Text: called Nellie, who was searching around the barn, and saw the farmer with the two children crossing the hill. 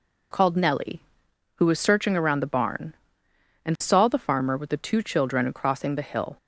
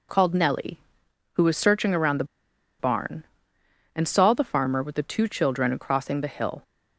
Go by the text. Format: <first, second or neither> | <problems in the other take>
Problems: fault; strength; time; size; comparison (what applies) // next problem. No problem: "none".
first | pauses between "the" and "barn"; noticeable; at 2.2 s; 0.55 s long